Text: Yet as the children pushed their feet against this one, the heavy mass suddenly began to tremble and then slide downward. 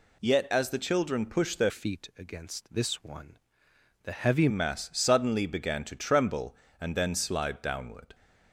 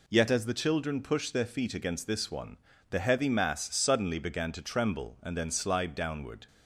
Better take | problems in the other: second | changes voice from "feet" to "heavy"; from 1.6 to 4.4 s; 2.8 s long

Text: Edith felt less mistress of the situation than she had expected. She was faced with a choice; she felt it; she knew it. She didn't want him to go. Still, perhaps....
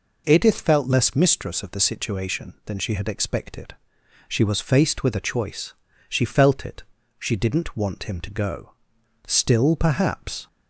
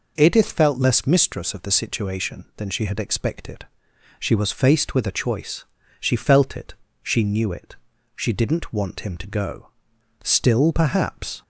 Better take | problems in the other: second | skips "she knew it"; at 7.0 s

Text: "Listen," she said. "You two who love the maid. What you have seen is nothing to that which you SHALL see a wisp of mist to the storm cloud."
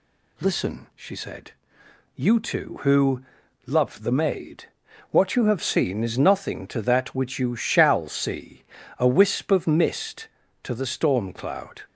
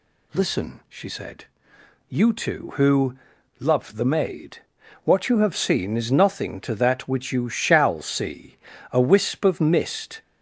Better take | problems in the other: first | pauses between "who" and "love"; at 3.1 s; 0.40 s long; also in the first // pauses between "see" and "a"; slight; at 8.5 s; 0.36 s long; slight in the first // stops before "to the storm cloud"; at 10.2 s

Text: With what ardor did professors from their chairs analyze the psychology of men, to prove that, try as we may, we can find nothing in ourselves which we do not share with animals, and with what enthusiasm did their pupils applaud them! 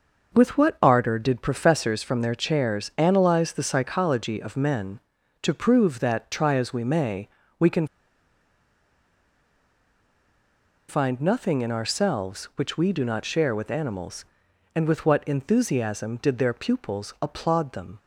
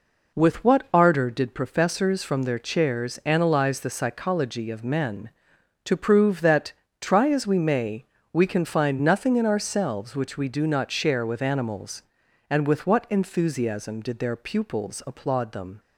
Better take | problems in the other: second | pauses between "can" and "find"; strong; at 7.8 s; 3.0 s long

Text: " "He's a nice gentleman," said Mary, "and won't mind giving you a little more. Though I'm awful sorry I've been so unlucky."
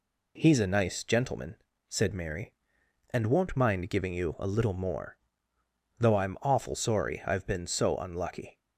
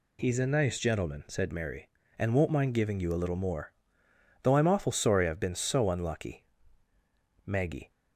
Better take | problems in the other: first | goes on to say "Maggie"; slight; from 7.4 s on; 0.44 s long

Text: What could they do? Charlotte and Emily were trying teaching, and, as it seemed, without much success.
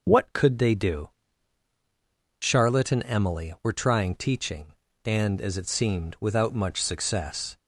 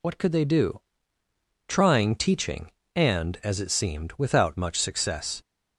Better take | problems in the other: first | skips "Charlotte and Emily were"; at 1.2 s

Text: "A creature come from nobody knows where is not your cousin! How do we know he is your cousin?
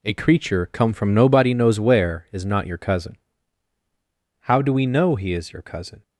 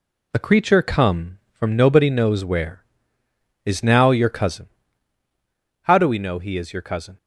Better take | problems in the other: first | says "now" for "not"; at 3.8 s

